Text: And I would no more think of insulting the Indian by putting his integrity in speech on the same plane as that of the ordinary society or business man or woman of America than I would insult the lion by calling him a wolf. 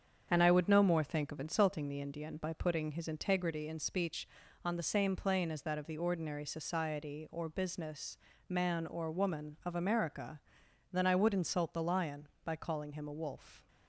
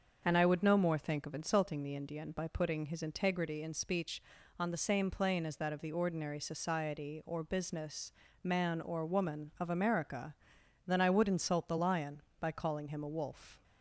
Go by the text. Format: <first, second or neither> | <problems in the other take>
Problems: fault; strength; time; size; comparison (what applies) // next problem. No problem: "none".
second | gets quieter; noticeable; throughout; 5 dB // starts louder than the rest; strong; until 1.3 s; 7.5 dB; also in the second // pauses between "business" and "man"; slight; at 8.1 s; 0.30 s long; slight in the second